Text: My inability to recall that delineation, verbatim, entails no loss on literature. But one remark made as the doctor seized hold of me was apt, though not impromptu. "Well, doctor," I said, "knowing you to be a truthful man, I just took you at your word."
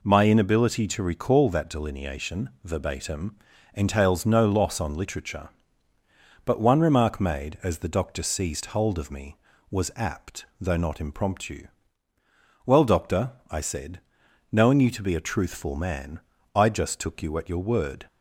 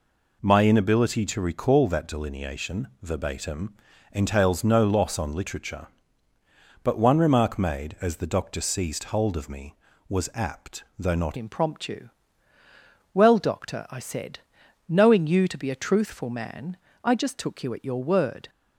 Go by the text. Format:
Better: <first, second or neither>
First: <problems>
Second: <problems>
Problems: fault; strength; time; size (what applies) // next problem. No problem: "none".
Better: first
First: none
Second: changes voice at "impromptu"; from 11.3 s on; 7.1 s long